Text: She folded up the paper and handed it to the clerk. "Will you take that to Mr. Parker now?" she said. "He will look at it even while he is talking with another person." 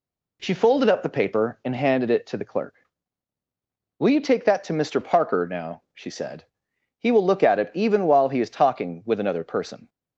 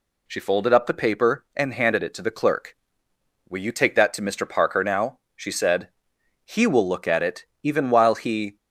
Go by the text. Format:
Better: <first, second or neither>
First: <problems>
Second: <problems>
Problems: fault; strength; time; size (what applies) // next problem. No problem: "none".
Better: first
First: none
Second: pauses between "it" and "even"; slight; at 7.4 s; 0.18 s long // stops before "is talking with another person"; at 8.5 s